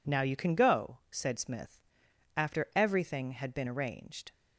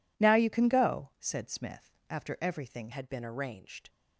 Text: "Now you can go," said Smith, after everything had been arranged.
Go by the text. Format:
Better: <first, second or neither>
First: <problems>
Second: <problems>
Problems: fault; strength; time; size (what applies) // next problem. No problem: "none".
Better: first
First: none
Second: changes voice at "had"; from 2.9 s on; 0.9 s long